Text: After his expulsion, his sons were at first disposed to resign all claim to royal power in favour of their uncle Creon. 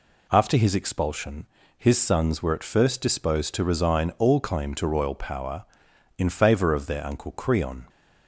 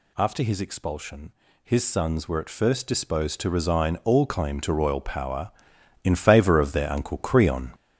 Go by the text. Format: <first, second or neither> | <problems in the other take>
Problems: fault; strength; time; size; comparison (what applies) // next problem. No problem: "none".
first | gets louder; throughout; 7 dB